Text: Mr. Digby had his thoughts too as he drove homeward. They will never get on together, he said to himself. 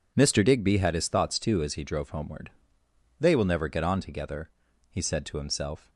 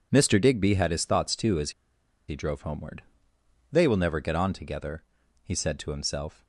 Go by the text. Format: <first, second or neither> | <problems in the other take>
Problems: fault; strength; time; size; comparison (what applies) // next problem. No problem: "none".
first | pauses between "as" and "he"; noticeable; at 1.7 s; 0.57 s long